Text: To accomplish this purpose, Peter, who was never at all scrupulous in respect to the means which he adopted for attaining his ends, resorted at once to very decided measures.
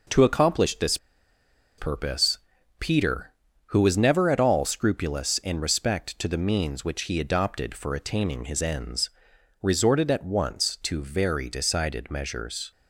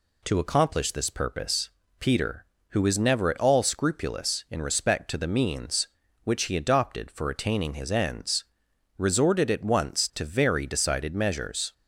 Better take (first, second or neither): second